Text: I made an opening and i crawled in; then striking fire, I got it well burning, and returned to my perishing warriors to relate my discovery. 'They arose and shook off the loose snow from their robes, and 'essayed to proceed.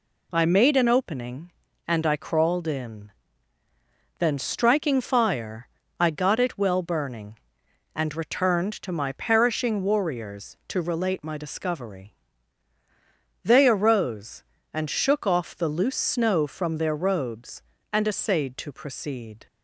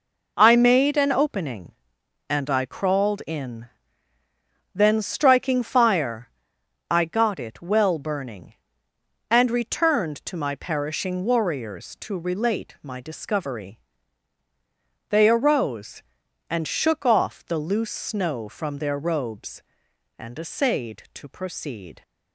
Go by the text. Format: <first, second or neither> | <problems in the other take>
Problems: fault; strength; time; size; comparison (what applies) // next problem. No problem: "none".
neither | none